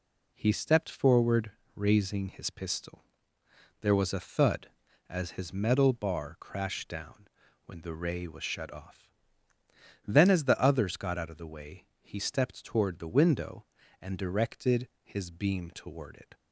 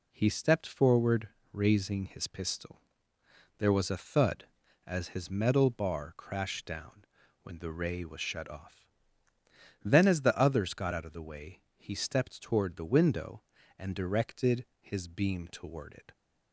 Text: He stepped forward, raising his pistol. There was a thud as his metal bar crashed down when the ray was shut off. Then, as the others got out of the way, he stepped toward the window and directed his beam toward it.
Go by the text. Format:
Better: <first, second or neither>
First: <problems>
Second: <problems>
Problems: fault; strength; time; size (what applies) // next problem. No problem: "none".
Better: neither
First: pauses between "down" and "when"; slight; at 7.2 s; 0.36 s long // pauses between "directed" and "his"; slight; at 14.8 s; 0.16 s long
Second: pauses between "down" and "when"; slight; at 7.0 s; 0.36 s long // pauses between "directed" and "his"; slight; at 14.6 s; 0.16 s long